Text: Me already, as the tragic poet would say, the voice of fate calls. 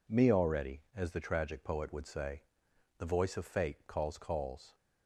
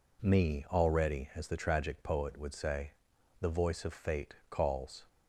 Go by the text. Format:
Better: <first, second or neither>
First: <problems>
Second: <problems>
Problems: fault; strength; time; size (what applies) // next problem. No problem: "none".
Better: second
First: says "calls" twice; at 4.1 s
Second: none